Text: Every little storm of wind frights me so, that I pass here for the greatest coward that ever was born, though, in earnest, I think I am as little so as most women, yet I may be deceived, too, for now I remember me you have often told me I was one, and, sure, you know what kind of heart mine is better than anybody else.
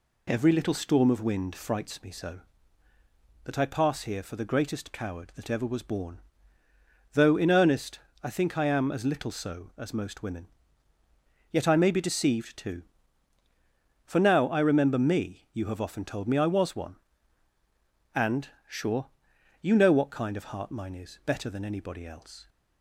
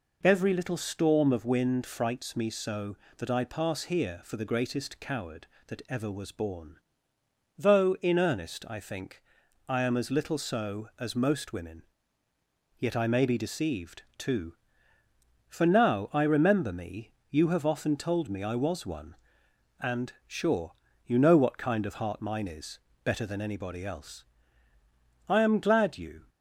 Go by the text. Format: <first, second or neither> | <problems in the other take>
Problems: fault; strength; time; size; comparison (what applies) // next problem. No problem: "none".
first | pauses between "think" and "I"; noticeable; at 9.2 s; 0.46 s long // pauses between "me" and "you"; slight; at 17.1 s; 0.18 s long // pauses between "is" and "better"; slight; at 22.7 s; 0.26 s long // goes on to say "I am glad you"; noticeable; from 25.2 s on; 1.0 s long